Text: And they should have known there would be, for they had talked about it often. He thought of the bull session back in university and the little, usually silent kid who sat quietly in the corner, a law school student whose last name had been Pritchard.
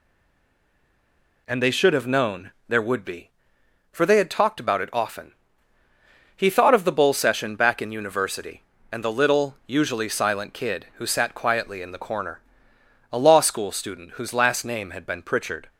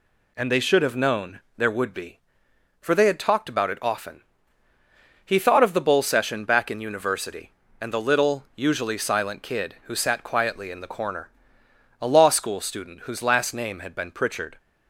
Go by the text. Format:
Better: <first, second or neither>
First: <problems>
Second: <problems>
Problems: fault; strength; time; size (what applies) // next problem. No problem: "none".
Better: second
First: stays silent before the first word; noticeable; until 1.4 s; 1.4 s long // pauses between "known" and "there"; slight; at 2.5 s; 0.18 s long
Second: pauses between "known" and "there"; slight; at 1.3 s; 0.18 s long